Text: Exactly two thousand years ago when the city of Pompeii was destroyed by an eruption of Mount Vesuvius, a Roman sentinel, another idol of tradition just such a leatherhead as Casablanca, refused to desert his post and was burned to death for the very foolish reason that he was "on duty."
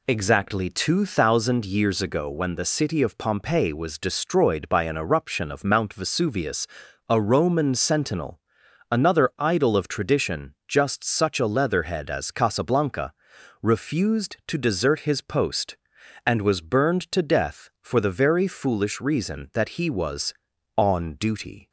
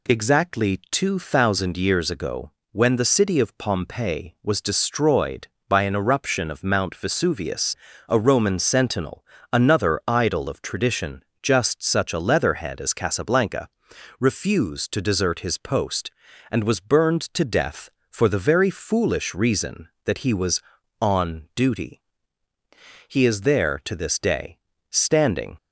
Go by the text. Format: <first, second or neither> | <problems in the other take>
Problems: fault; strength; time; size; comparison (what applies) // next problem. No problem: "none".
first | pauses between "ago" and "when"; slight; at 2.5 s; 0.20 s long // pauses between "tradition" and "just"; slight; at 11.2 s; 0.18 s long // goes on to say "He is there to this day standing"; strong; from 23.0 s on; 2.4 s long